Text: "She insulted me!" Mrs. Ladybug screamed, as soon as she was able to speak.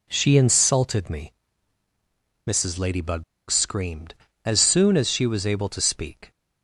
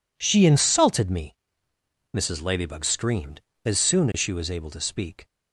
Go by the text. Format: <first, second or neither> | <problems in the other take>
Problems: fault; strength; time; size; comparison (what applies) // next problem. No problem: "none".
second | pauses between "Ladybug" and "screamed"; slight; at 3.2 s; 0.26 s long